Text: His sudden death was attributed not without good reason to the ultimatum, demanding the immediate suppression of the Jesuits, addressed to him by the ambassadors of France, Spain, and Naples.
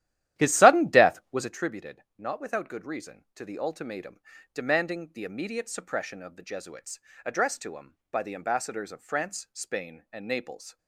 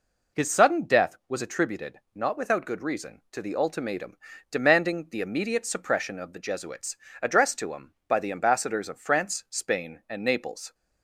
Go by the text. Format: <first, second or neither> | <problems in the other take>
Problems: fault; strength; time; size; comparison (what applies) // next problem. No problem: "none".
second | starts louder than the rest; strong; until 1.6 s; 13 dB